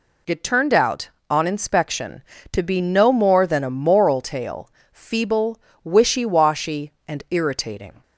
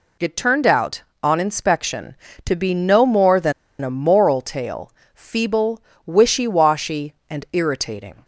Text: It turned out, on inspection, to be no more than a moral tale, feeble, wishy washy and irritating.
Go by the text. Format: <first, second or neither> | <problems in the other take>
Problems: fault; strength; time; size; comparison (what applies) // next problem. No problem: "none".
first | pauses between "than" and "a"; slight; at 3.5 s; 0.29 s long